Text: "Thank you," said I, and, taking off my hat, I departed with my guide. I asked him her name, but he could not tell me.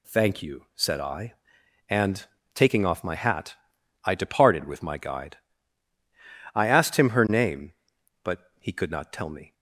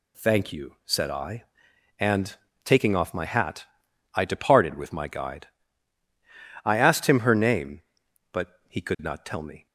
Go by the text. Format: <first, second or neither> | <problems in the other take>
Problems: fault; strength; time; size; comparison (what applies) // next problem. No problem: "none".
neither | none